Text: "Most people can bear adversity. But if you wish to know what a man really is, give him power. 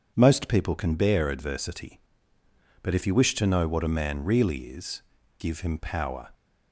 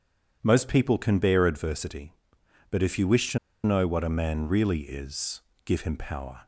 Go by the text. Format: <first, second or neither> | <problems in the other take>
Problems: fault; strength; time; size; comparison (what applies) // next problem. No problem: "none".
first | pauses between "to" and "know"; slight; at 3.3 s; 0.26 s long